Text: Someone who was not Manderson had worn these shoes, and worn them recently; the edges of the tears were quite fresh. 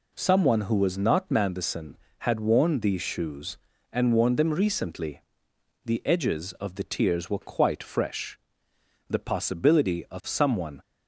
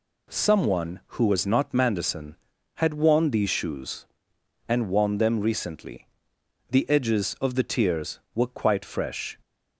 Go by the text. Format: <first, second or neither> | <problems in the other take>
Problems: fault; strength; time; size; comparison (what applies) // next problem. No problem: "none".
second | goes on to say "The possibility of someone"; strong; from 9.0 s on; 1.7 s long